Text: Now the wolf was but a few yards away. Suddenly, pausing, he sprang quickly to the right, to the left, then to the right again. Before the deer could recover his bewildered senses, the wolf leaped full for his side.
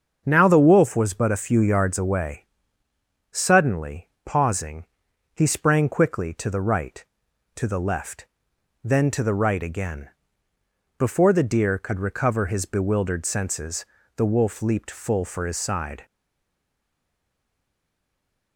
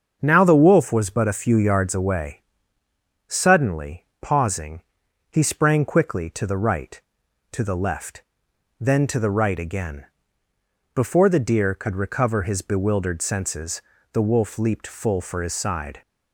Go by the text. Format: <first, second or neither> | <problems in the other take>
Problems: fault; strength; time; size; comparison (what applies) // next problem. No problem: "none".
second | starts louder than the rest; until 1.2 s; 6.5 dB; also in the second // stays silent after the last word; from 16.0 s on; 2.5 s long